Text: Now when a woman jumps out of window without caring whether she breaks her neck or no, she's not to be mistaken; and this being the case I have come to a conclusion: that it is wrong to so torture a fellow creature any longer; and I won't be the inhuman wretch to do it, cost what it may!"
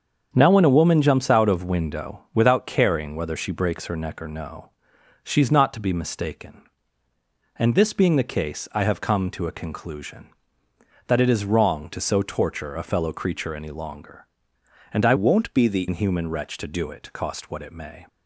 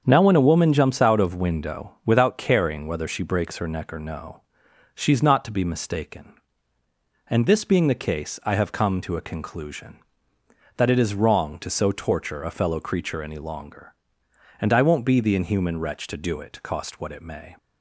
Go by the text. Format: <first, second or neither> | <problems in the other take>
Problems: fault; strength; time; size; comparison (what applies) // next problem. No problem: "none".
second | starts louder than the rest; strong; until 1.3 s; 7 dB; strong in the second // changes voice from "won't" to "the"; from 15.1 to 15.8 s; 0.7 s long